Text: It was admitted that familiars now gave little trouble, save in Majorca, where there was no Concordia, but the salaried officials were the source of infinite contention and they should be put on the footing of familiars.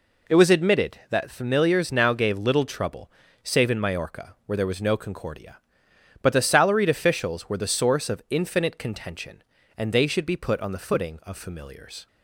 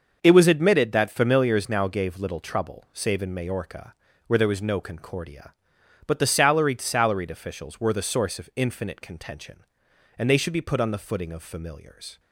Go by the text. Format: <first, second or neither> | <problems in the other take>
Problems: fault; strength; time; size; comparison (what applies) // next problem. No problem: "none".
first | starts louder than the rest; until 1.2 s; 6.5 dB // says "salaried" twice; at 6.8 s